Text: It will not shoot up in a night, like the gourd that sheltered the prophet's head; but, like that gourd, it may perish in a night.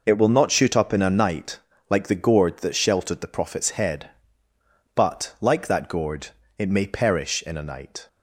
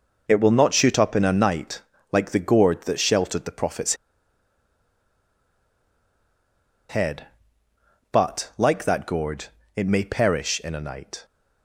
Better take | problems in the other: first | pauses between "prophet's" and "head"; strong; at 3.9 s; 2.9 s long

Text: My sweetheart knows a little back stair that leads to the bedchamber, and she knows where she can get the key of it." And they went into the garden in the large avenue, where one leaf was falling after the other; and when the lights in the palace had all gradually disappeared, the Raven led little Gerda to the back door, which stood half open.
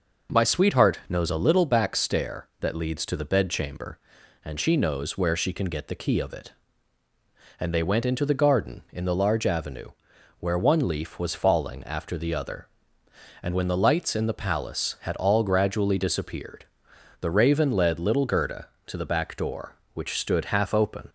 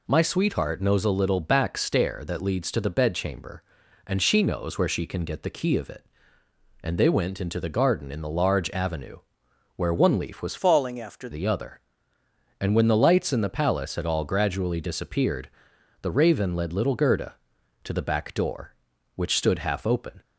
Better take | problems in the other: first | changes voice from "falling" to "after"; from 10.5 to 11.2 s; 0.7 s long

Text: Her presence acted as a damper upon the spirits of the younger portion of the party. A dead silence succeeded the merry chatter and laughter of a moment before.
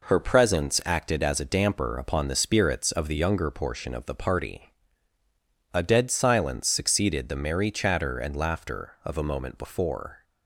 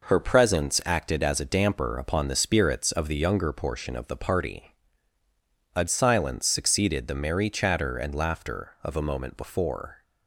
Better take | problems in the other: first | skips "dead"; at 5.8 s

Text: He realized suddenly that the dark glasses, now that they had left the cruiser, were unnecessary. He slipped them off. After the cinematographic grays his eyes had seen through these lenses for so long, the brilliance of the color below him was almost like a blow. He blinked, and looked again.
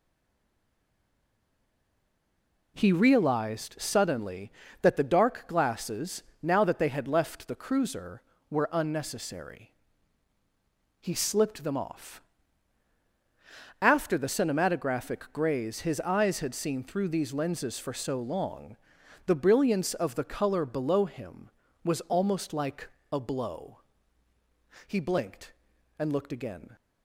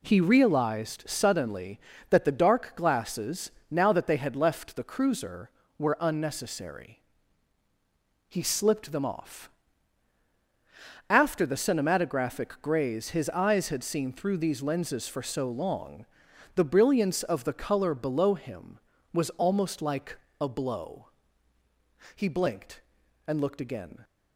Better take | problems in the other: second | stays silent before the first word; strong; until 2.7 s; 2.7 s long // pauses between "like" and "a"; slight; at 22.8 s; 0.24 s long; slight in the second

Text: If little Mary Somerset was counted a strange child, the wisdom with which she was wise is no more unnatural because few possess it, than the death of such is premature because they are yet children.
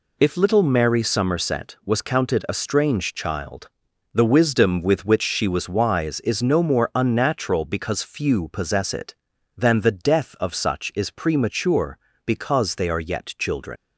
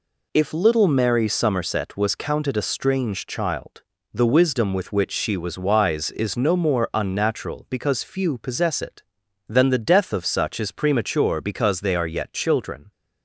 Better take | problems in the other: second | leaves "children" unfinished; at 13.7 s; 120 ms

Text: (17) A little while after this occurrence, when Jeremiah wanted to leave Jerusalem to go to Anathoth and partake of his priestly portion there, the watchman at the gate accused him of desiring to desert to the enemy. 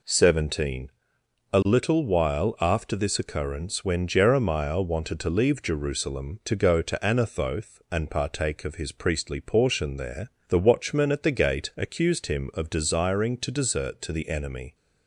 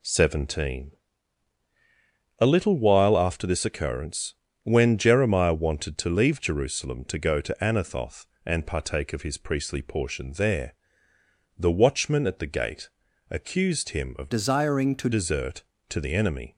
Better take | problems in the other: first | pauses between "gate" and "accused"; at 12.8 s; 0.40 s long // changes voice from "desiring" to "to"; from 14.3 to 15.0 s; 0.7 s long

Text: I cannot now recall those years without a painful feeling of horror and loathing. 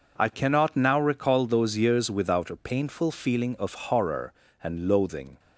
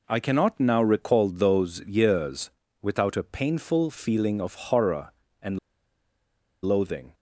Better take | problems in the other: first | pauses between "years" and "without"; slight; at 2.5 s; 0.32 s long // pauses between "and" and "loathing"; at 5.5 s; 1.0 s long

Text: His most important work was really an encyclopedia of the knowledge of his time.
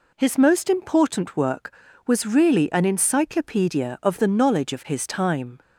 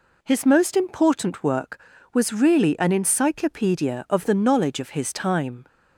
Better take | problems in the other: neither | none

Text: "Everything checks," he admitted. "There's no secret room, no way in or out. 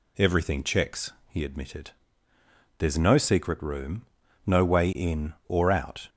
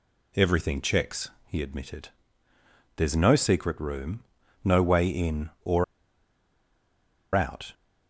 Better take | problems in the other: first | pauses between "or" and "out"; strong; at 5.8 s; 1.5 s long

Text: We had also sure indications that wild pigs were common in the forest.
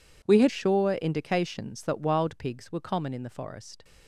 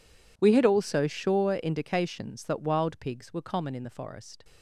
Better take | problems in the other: second | skips "also"; at 0.4 s

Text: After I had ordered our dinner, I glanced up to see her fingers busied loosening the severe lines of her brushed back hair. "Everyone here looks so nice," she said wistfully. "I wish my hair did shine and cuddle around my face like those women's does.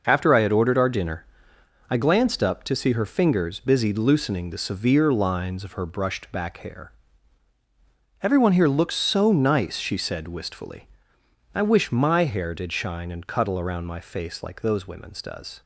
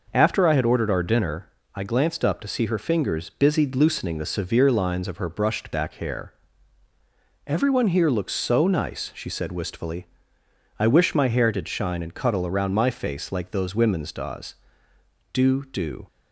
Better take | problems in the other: first | goes on to say "Do do"; noticeable; from 15.3 s on; 0.72 s long

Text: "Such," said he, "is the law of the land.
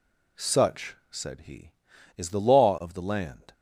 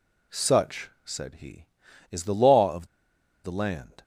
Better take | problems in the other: first | pauses between "of" and "the"; noticeable; at 2.8 s; 0.58 s long

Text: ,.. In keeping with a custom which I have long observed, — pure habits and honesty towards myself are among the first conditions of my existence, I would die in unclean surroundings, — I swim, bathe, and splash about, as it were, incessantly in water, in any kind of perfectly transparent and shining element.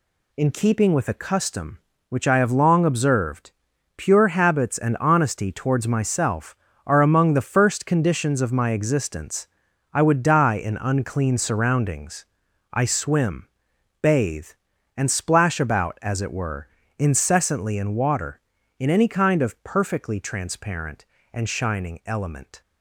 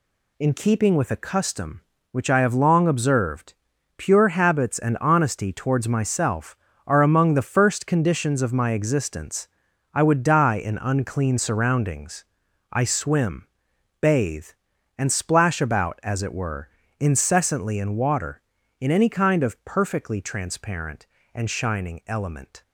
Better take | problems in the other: neither | none

